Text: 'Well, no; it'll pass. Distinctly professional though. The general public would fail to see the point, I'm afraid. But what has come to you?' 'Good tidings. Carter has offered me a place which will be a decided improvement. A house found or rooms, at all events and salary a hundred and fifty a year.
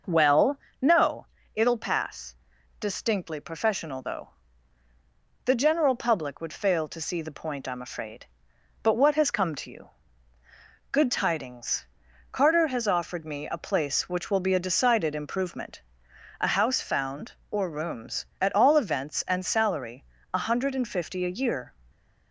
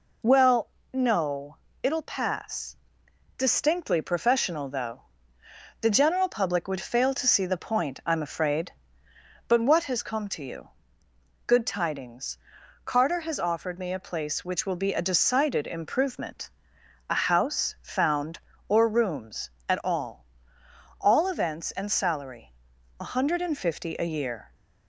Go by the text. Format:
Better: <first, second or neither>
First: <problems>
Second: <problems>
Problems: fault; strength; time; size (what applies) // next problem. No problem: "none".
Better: first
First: pauses between "salary" and "a"; slight; at 20.0 s; 0.30 s long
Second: says "all" twice; at 21.0 s // pauses between "salary" and "a"; at 22.5 s; 0.44 s long